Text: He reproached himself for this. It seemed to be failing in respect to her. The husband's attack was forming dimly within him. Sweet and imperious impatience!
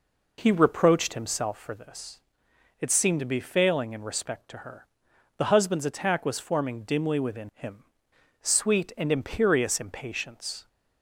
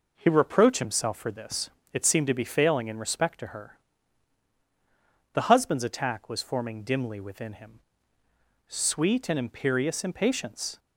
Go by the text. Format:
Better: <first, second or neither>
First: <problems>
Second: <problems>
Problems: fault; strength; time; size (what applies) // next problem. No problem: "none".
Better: neither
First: none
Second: none